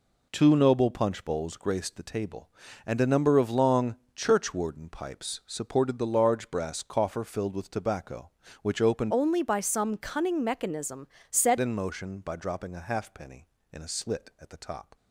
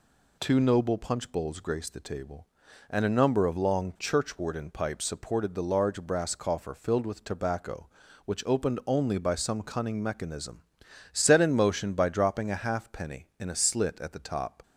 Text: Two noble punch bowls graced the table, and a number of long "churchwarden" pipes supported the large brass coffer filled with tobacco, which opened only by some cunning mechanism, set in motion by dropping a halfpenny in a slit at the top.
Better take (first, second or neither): second